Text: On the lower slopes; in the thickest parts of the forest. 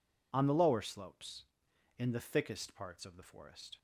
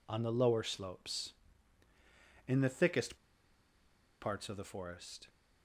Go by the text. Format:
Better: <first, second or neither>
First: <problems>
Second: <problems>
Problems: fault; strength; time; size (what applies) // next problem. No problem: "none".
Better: first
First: none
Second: pauses between "thickest" and "parts"; at 3.1 s; 1.0 s long